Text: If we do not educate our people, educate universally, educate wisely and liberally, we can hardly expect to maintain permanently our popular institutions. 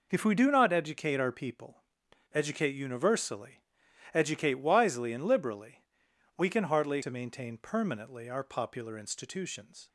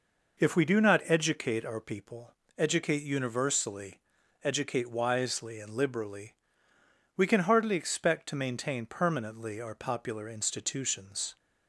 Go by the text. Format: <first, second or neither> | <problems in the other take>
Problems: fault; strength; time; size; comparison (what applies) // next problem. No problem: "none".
second | skips "expect"; at 7.0 s